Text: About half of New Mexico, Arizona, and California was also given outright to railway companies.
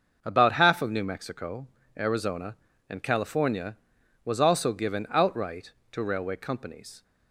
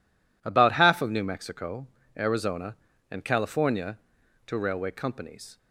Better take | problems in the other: first | skips "was also given outright"; at 4.2 s

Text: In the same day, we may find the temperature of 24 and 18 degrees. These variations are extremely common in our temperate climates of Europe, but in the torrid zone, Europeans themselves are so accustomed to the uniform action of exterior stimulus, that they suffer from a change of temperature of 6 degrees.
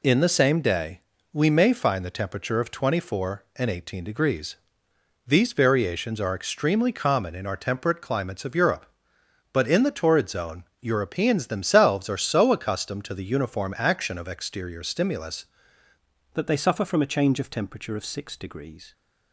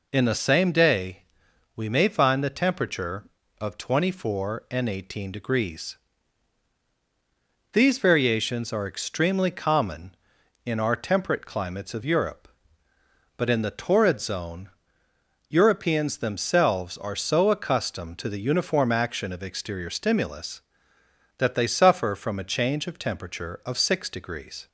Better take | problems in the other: second | changes voice at "that"; from 16.3 s on; 2.6 s long

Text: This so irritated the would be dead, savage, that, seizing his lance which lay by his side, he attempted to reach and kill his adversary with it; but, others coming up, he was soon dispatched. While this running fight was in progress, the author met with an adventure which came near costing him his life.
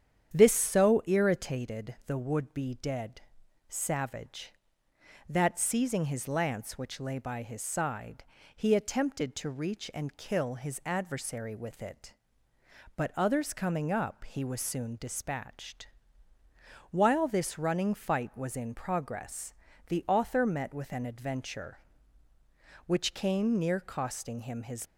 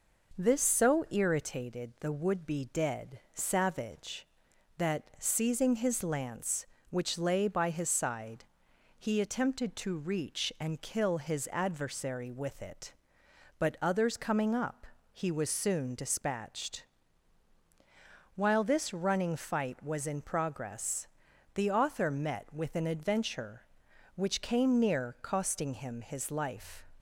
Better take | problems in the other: second | starts louder than the rest; strong; until 1.3 s; 9 dB // stops before "life"; at 24.8 s

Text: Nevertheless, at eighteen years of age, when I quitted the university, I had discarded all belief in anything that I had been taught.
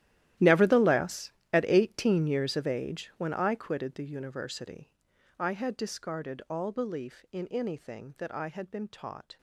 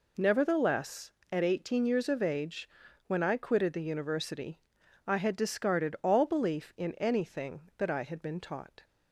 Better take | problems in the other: second | gets quieter; strong; throughout; 17.5 dB

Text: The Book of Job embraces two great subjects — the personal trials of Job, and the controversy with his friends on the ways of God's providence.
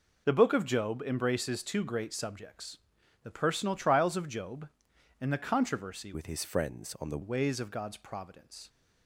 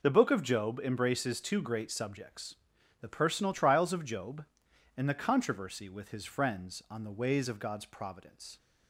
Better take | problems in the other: second | changes voice from "with" to "the"; from 6.1 to 7.1 s; 1.0 s long

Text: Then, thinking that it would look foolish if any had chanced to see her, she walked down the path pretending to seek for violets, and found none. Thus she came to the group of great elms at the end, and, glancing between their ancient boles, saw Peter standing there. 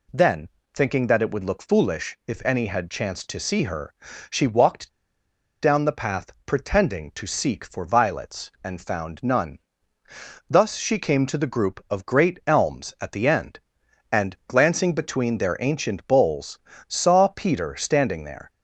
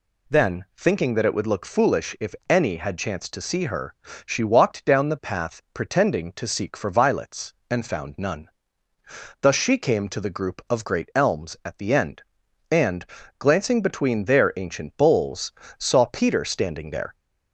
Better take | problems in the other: second | pauses between "walked" and "down"; noticeable; at 4.8 s; 0.70 s long

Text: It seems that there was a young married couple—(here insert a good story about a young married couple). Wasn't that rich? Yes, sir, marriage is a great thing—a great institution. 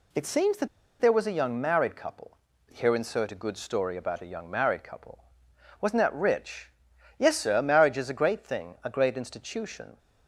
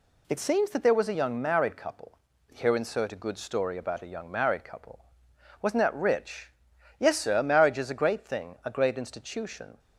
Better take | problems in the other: second | pauses between "that" and "there"; slight; at 0.6 s; 0.33 s long

